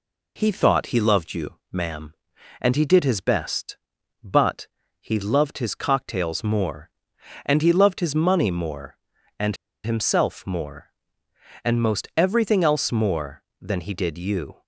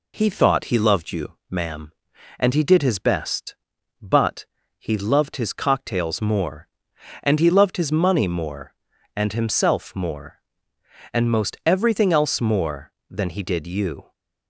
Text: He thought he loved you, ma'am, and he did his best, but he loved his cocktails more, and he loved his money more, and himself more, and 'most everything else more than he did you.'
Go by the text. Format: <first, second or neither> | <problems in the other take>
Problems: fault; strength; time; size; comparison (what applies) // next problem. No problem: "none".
second | pauses between "but" and "he"; slight; at 4.6 s; 0.34 s long; slight in the second // pauses between "and" and "himself"; slight; at 9.5 s; 0.28 s long